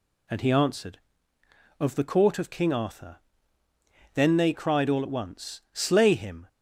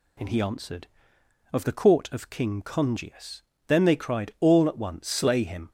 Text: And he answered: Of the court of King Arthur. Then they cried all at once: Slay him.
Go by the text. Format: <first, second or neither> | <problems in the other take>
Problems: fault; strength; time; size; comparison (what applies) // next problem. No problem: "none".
first | says "Congius" for "Arthur"; at 2.6 s